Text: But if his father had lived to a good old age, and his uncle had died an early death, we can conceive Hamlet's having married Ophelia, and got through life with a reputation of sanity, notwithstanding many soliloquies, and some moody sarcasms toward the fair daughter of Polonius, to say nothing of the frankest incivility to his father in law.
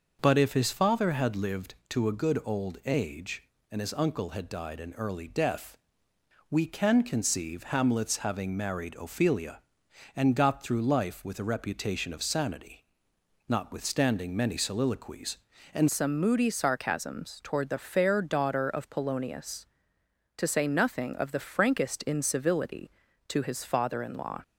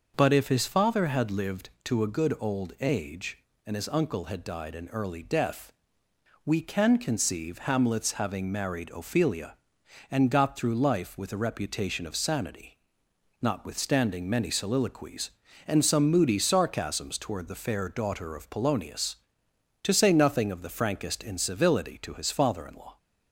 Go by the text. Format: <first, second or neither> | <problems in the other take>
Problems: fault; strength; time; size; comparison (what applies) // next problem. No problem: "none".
second | changes voice at "some"; from 15.8 s on; 8.6 s long